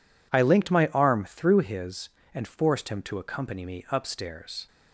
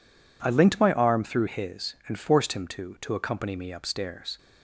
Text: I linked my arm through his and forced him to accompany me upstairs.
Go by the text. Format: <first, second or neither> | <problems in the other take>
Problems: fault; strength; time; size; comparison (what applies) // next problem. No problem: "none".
first | says "to" twice; at 3.0 s